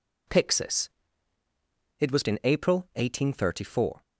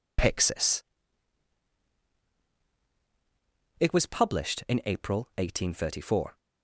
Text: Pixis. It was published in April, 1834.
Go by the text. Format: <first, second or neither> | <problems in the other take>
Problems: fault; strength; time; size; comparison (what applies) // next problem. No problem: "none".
second | skips "published"; at 2.2 s